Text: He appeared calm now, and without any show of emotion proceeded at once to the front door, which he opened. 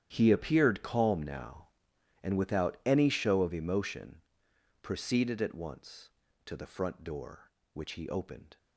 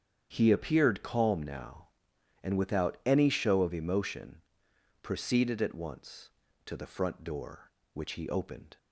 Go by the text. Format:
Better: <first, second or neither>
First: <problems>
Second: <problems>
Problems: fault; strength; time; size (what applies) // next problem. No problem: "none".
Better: second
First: gets quieter; strong; throughout; 16.5 dB // starts louder than the rest; strong; until 1.1 s; 10 dB // pauses between "emotion" and "proceeded"; noticeable; at 4.1 s; 0.62 s long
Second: starts louder than the rest; strong; until 1.3 s; 8 dB // pauses between "emotion" and "proceeded"; noticeable; at 4.3 s; 0.62 s long